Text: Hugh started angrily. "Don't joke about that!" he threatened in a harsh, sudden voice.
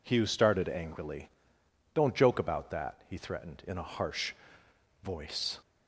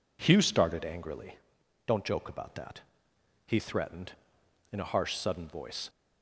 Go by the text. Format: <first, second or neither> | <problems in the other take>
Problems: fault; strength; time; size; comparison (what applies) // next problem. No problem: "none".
second | skips "sudden"; at 4.6 s